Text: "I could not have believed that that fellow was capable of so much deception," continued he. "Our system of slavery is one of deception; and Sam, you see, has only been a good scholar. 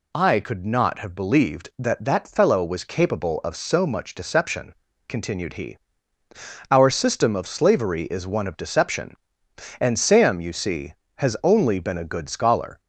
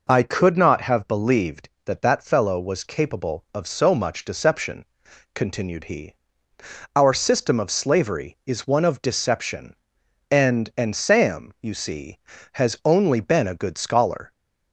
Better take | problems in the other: first | says "and" twice; at 10.7 s

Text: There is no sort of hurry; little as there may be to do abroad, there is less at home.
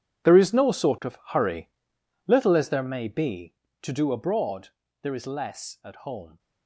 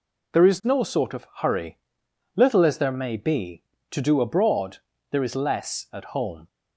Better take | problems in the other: second | gets quieter; strong; throughout; 16 dB

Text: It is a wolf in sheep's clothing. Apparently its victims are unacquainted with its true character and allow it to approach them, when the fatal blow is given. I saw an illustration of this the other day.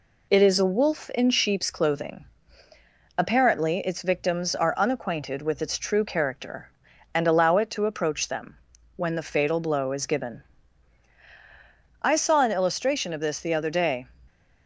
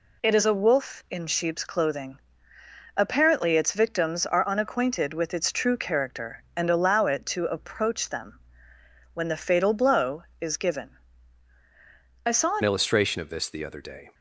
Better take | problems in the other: first | changes voice at "illustration"; from 12.6 s on; 1.5 s long

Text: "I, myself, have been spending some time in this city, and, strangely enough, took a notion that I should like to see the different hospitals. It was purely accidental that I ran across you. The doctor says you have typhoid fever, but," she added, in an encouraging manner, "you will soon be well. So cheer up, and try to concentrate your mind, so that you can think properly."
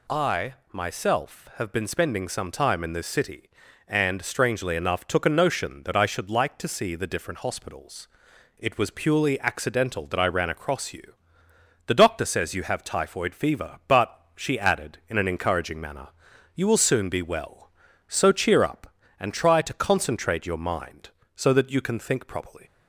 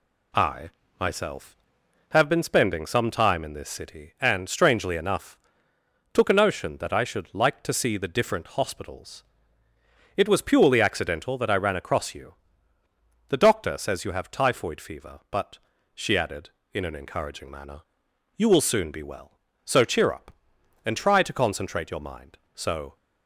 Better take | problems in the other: first | stops before "that you can think properly"; at 22.9 s

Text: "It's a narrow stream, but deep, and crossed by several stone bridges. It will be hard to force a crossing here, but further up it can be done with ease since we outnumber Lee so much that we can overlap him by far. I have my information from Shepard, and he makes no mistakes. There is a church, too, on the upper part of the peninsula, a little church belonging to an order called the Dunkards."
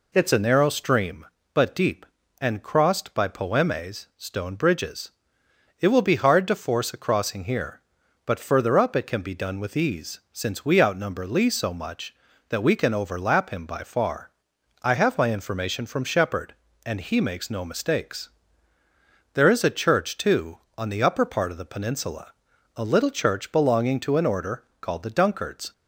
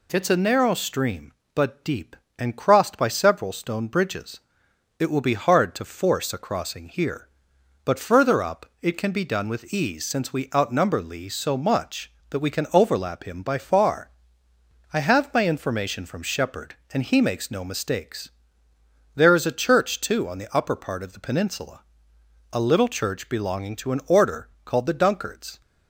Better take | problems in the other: second | says "poemes" for "several"; at 3.2 s // pauses between "order" and "called"; slight; at 24.6 s; 0.20 s long; slight in the second

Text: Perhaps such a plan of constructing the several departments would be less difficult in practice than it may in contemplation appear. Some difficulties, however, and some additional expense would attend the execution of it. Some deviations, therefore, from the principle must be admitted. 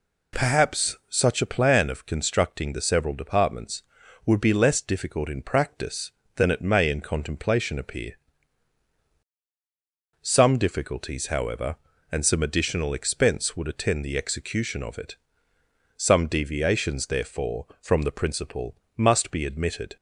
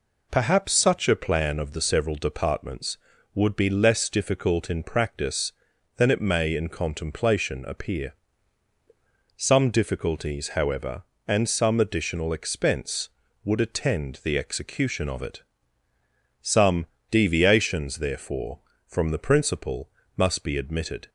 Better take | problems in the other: first | skips "constructing"; at 1.7 s // pauses between "Some" and "deviations"; slight; at 16.8 s; 0.24 s long // pauses between "principle" and "must"; slight; at 19.8 s; 0.28 s long; slight in the first

